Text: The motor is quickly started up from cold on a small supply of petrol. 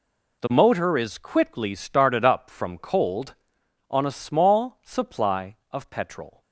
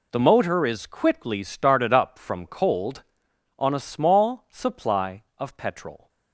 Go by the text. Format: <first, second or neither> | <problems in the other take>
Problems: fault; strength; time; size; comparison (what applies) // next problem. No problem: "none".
neither | none